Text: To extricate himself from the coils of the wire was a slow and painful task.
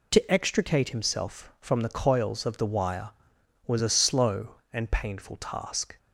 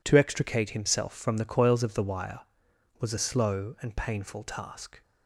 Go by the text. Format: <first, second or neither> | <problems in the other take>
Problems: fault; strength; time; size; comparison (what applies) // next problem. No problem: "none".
neither | none